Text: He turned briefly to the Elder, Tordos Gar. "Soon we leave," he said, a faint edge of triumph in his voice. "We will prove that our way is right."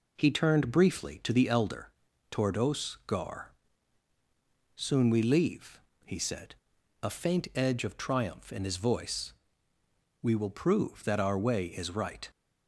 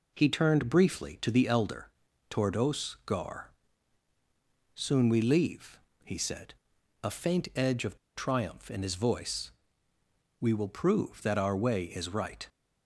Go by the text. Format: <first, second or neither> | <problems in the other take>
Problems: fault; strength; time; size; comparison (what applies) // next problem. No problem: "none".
first | pauses between "of" and "triumph"; slight; at 7.9 s; 0.18 s long